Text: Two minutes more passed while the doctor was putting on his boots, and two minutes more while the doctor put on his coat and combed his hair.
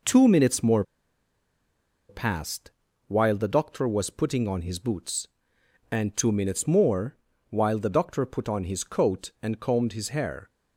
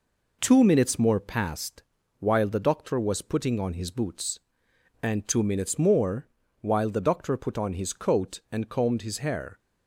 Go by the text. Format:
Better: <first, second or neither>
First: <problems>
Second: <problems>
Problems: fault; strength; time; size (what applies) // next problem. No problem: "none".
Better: second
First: pauses between "more" and "passed"; strong; at 0.8 s; 1.2 s long // pauses between "passed" and "while"; at 2.7 s; 0.38 s long // pauses between "more" and "while"; slight; at 7.1 s; 0.32 s long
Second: pauses between "passed" and "while"; at 1.8 s; 0.38 s long // pauses between "more" and "while"; slight; at 6.2 s; 0.32 s long